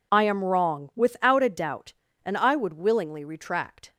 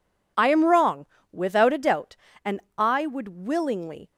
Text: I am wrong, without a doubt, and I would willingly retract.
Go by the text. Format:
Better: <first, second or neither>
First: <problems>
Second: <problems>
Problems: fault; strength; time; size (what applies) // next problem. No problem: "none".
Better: first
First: none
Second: pauses between "and" and "I"; slight; at 2.6 s; 0.16 s long // stops before "retract"; at 4.1 s